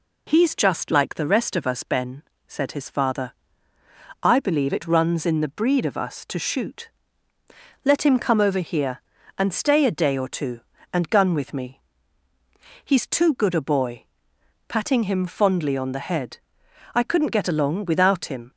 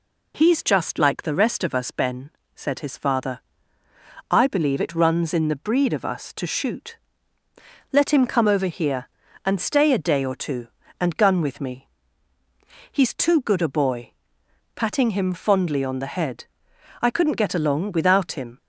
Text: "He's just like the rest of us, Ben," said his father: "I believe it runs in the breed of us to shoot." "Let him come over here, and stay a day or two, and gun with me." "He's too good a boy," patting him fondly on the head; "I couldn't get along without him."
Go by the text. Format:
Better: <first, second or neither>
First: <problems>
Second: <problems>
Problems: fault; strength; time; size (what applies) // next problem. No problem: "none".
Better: neither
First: none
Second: none